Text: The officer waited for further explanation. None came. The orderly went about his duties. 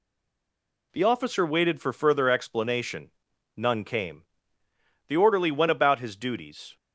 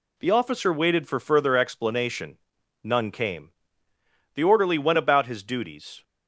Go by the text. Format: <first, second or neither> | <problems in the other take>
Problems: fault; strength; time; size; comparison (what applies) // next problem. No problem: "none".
second | stays silent before the first word; slight; until 0.9 s; 0.9 s long